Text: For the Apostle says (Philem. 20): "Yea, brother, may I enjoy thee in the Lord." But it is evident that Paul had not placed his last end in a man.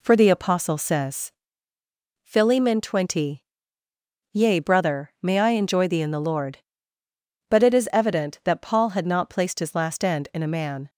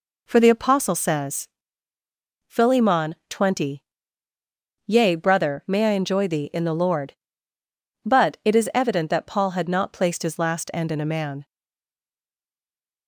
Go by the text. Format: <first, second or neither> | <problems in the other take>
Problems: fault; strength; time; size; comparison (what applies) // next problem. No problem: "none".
first | stays silent after the last word; noticeable; from 11.4 s on; 1.6 s long